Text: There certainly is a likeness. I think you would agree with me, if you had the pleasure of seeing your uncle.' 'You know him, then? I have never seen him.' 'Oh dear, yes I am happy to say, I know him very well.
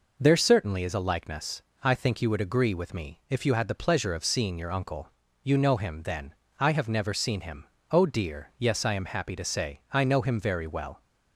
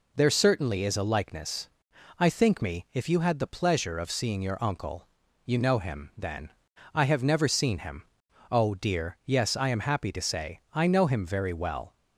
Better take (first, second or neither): first